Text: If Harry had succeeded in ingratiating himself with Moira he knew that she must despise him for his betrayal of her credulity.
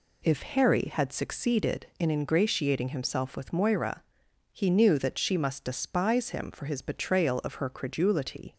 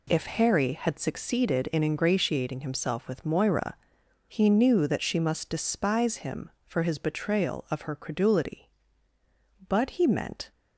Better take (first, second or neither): first